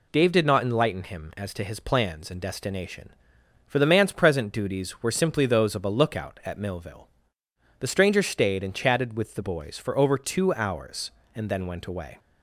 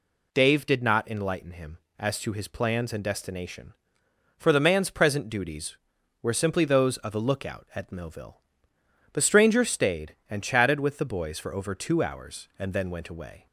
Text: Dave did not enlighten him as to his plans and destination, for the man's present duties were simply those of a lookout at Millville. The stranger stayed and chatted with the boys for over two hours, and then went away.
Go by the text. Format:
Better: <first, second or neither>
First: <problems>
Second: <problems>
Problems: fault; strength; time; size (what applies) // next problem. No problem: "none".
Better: neither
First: none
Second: none